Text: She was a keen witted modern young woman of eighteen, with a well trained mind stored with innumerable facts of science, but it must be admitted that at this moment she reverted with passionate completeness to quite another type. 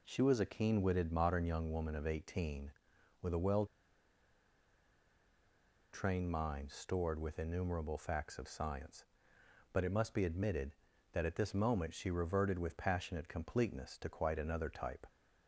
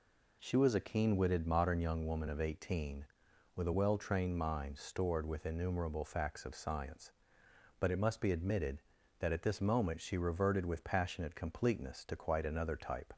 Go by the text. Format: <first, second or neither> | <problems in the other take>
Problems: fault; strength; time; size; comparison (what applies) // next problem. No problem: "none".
second | pauses between "well" and "trained"; strong; at 3.6 s; 2.2 s long